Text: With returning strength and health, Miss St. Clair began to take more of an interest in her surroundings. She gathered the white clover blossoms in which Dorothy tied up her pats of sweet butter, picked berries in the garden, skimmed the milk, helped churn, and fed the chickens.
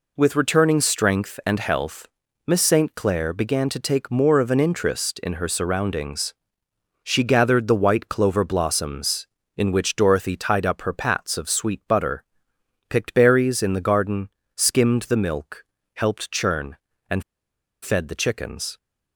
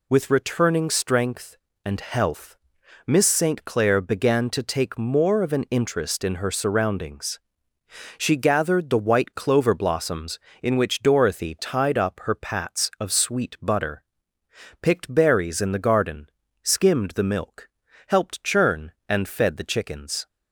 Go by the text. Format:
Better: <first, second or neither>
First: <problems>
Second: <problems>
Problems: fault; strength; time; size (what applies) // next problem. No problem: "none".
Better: second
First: pauses between "and" and "fed"; noticeable; at 17.2 s; 0.59 s long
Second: none